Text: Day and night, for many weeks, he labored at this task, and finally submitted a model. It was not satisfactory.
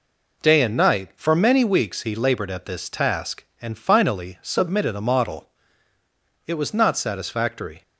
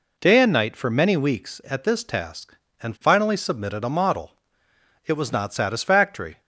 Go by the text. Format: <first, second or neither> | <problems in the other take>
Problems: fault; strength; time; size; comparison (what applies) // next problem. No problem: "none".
first | skips "he labored"; at 1.6 s